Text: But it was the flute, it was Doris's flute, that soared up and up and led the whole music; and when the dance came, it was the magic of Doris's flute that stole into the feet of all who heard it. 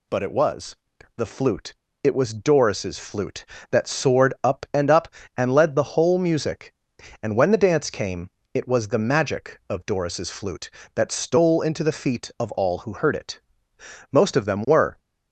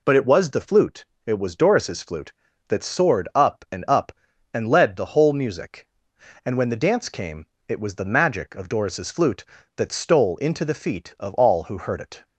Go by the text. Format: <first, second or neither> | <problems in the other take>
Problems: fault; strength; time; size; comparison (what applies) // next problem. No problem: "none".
second | pauses between "was" and "the"; at 0.7 s; 0.44 s long // goes on to say "Most of them were"; noticeable; from 14.0 s on; 0.88 s long